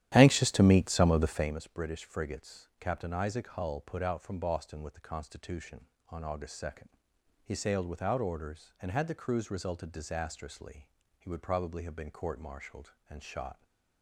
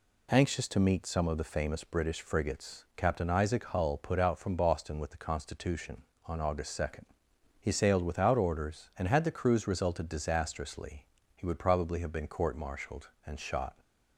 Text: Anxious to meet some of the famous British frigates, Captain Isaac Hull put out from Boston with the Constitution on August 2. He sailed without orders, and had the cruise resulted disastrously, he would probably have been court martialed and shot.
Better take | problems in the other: second | starts louder than the rest; strong; until 1.5 s; 12 dB

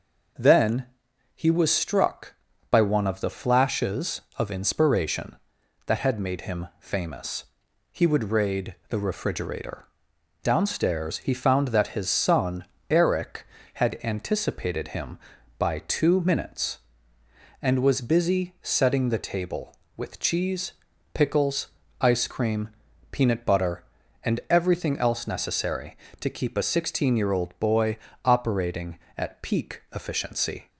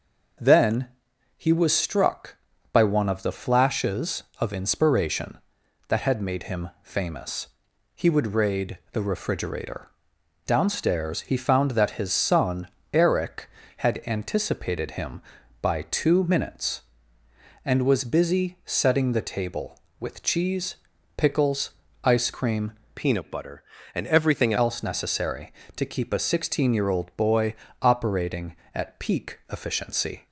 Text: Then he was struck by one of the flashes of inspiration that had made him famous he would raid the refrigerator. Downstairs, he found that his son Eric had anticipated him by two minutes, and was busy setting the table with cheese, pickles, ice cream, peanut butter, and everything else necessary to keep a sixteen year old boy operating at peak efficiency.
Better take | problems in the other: first | pauses between "Then" and "he"; noticeable; at 0.8 s; 0.50 s long; noticeable in the first // pauses between "famous" and "he"; noticeable; at 7.4 s; 0.50 s long; noticeable in the first // pauses between "son" and "Eric"; slight; at 12.6 s; 0.24 s long; slight in the first // changes voice from "peanut" to "everything"; from 22.9 to 24.5 s; 1.6 s long // pauses between "boy" and "operating"; slight; at 27.5 s; 0.26 s long; slight in the first

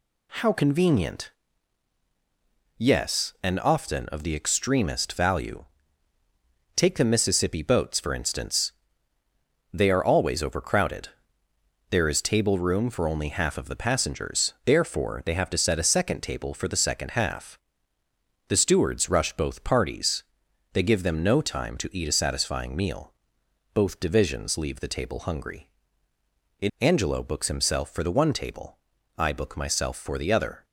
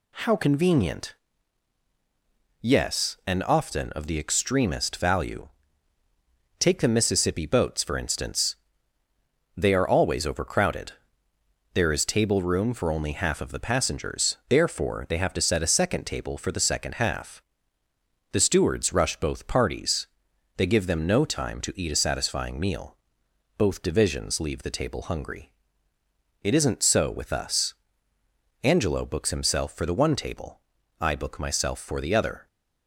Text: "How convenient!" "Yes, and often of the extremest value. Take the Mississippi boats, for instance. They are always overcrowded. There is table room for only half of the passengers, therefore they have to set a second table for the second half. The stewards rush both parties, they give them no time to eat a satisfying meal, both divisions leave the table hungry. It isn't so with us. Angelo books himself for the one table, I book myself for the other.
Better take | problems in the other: second | skips "isn't so with us"; at 26.7 s

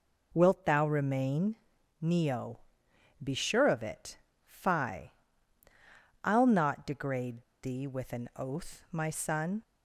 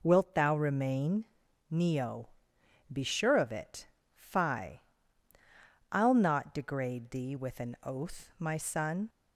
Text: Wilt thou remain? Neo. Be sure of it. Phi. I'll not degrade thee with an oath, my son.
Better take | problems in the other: second | pauses between "degrade" and "thee"; slight; at 7.4 s; 0.20 s long

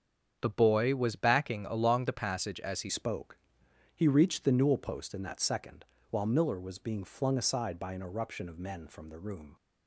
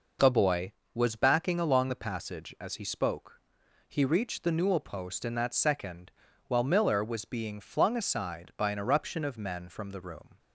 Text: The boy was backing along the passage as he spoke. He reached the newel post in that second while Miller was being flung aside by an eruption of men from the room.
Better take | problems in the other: second | starts louder than the rest; strong; until 1.4 s; 7.5 dB // changes voice at "spoke"; from 2.8 s on; 6.7 s long // pauses between "second" and "while"; slight; at 5.8 s; 0.28 s long; also in the second

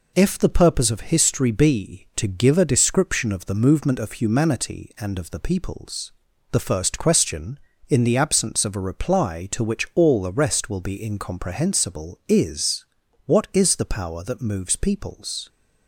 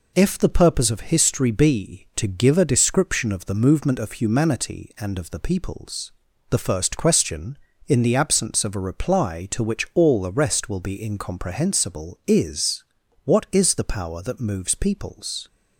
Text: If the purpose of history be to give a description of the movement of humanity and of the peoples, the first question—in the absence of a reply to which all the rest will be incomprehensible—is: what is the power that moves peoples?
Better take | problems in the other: neither | none

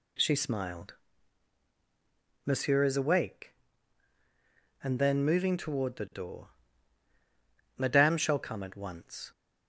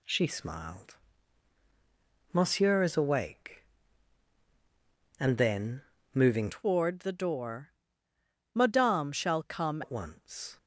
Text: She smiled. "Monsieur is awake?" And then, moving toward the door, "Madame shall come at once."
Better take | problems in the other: first | changes voice from "toward" to "come"; from 6.5 to 9.8 s; 3.3 s long

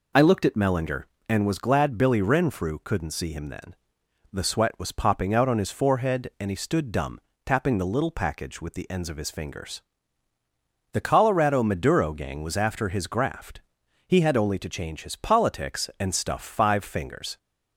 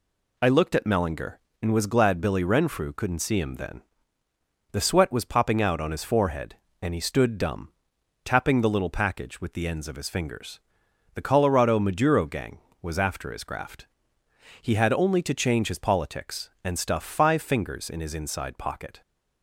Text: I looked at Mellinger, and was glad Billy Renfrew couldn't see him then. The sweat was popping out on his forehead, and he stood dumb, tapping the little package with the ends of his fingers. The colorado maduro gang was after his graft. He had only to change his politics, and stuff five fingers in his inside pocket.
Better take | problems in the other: second | stops before "in his inside pocket"; at 17.3 s

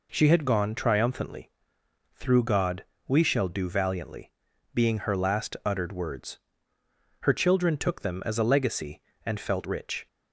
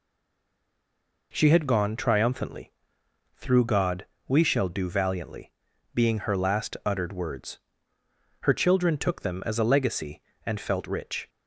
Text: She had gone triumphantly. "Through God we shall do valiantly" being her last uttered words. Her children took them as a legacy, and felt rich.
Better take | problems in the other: first | stays silent before the first word; noticeable; until 1.3 s; 1.3 s long // pauses between "God" and "we"; slight; at 4.0 s; 0.22 s long; slight in the first // pauses between "valiantly" and "being"; at 5.5 s; 0.42 s long; also in the first

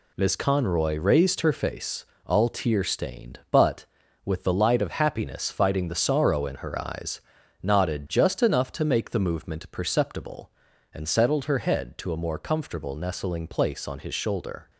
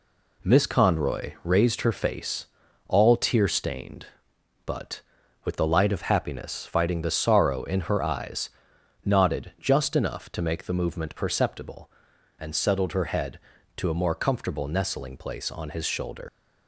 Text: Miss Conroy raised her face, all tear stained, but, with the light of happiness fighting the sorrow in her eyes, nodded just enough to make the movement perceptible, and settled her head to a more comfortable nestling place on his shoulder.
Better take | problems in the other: first | leaves "shoulder" unfinished; at 16.2 s; 95 ms

